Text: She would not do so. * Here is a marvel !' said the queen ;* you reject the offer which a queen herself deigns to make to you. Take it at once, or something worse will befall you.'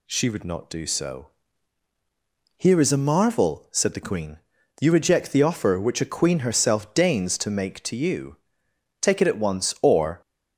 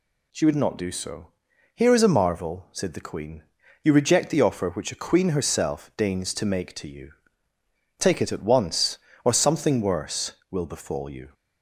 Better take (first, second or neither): second